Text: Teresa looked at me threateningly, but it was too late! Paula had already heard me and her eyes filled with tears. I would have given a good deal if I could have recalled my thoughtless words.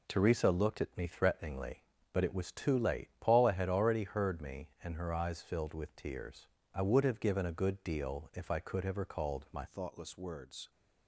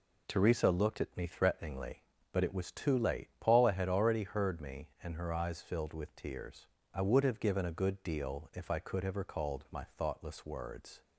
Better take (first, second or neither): second